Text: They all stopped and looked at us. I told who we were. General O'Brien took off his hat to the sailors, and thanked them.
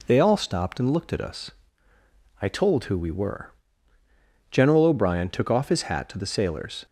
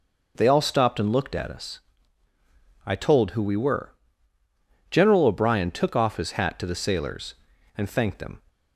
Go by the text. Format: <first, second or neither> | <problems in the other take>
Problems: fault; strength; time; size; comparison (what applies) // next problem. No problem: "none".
second | stops before "and thanked them"; at 6.8 s